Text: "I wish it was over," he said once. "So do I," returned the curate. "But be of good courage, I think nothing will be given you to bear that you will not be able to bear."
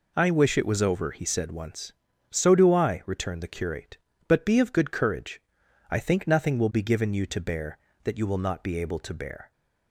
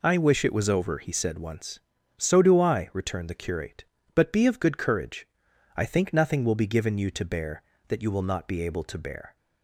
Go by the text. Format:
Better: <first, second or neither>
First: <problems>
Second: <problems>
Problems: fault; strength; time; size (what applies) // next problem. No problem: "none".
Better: neither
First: none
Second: none